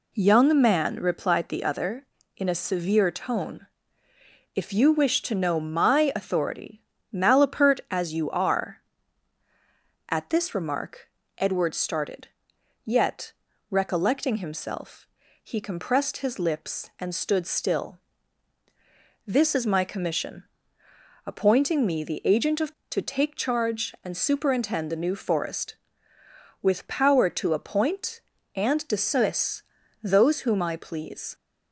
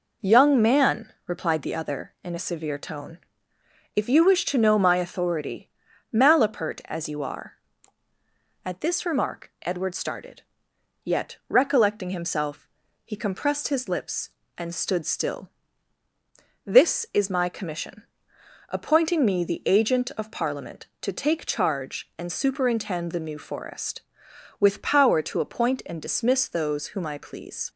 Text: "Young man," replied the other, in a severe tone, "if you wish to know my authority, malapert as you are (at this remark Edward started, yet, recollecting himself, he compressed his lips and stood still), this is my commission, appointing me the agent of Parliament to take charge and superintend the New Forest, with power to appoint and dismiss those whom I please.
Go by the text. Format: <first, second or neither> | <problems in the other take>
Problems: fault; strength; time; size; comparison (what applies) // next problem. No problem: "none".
second | pauses between "remark" and "Edward"; slight; at 11.0 s; 0.30 s long // skips "Parliament"; at 22.8 s // pauses between "dismiss" and "those"; at 29.6 s; 0.38 s long